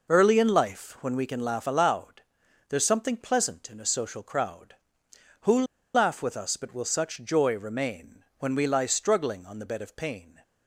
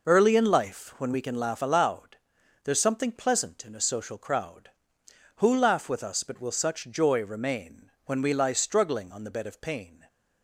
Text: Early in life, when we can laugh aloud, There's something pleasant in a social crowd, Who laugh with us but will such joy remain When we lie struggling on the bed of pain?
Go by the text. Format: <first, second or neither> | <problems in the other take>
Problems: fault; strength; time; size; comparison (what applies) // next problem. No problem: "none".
second | pauses between "Who" and "laugh"; slight; at 5.6 s; 0.30 s long